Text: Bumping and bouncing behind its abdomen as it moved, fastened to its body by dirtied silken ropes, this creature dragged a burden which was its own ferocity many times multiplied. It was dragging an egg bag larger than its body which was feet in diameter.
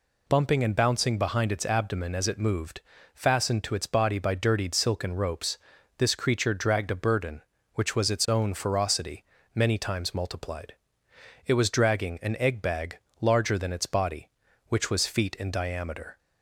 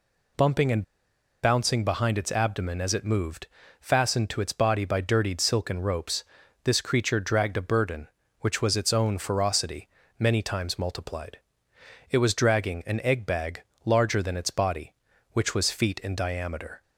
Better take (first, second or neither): first